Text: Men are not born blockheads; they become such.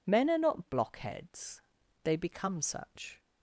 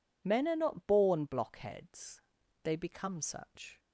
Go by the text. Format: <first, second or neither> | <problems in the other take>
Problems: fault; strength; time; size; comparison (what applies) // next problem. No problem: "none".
second | skips "born"; at 0.6 s